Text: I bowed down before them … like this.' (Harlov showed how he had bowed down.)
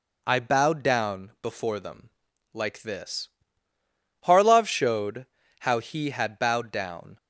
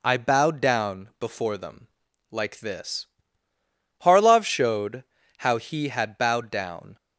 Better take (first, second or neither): neither